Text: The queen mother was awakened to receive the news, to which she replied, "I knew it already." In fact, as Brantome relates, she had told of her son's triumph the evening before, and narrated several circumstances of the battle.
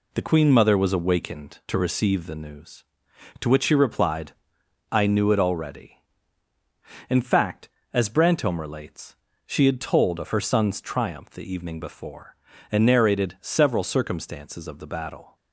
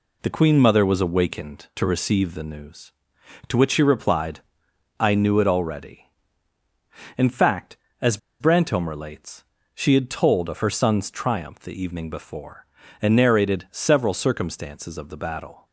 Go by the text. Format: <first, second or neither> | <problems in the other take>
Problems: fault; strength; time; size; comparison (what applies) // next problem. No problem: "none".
first | pauses between "as" and "Brantome"; slight; at 8.1 s; 0.22 s long